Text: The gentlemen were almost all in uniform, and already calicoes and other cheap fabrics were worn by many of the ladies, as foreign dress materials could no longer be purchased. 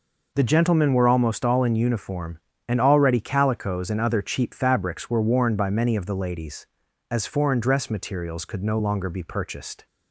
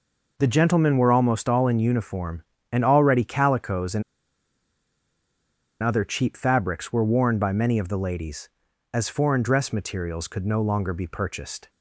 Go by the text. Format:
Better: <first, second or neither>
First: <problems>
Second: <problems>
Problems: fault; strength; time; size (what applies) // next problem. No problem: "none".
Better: first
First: none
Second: pauses between "and" and "other"; strong; at 4.0 s; 1.7 s long